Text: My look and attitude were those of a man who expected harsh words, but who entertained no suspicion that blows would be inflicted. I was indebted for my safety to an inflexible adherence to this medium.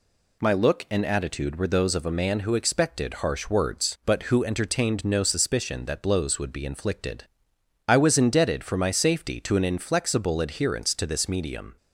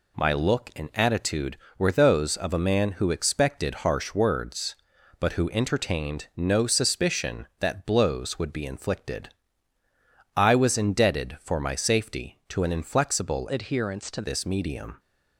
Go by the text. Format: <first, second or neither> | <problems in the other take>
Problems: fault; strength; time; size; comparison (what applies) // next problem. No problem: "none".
first | changes voice from "adherence" to "to"; from 13.4 to 14.2 s; 0.8 s long